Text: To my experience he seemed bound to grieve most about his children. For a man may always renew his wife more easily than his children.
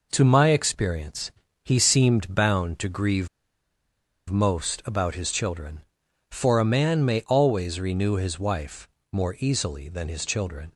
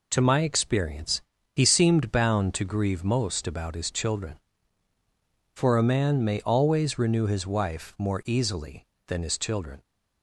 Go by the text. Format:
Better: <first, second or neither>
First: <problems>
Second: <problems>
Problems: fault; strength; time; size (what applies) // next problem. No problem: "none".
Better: second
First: pauses between "experience" and "he"; slight; at 1.3 s; 0.32 s long // pauses between "grieve" and "most"; at 3.2 s; 1.0 s long // pauses between "wife" and "more"; slight; at 8.8 s; 0.24 s long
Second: pauses between "experience" and "he"; slight; at 1.2 s; 0.32 s long